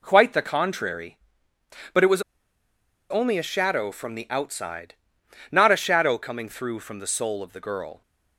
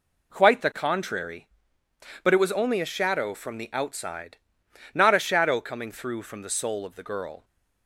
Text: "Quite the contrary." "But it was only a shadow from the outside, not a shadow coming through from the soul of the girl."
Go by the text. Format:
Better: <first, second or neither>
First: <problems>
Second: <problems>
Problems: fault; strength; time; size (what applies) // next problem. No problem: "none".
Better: second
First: pauses between "was" and "only"; noticeable; at 2.2 s; 0.89 s long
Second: none